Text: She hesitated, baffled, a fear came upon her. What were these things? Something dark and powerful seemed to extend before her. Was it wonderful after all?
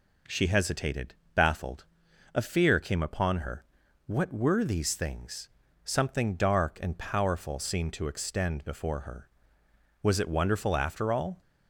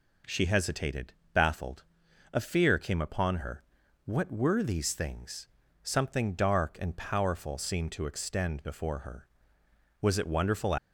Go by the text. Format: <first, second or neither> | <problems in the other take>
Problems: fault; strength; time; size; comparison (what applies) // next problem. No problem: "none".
first | stops before "after all"; at 10.7 s